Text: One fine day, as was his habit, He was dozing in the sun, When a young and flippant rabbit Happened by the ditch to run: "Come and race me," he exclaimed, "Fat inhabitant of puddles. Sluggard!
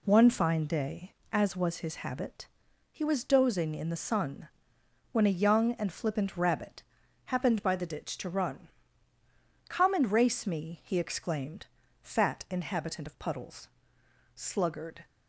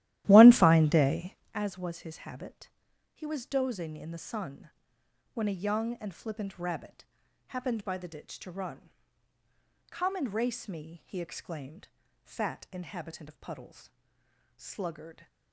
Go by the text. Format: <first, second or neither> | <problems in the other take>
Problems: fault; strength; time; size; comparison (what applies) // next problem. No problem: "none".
first | starts louder than the rest; strong; until 1.6 s; 14 dB // pauses between "rabbit" and "Happened"; at 7.0 s; 0.44 s long; also in the first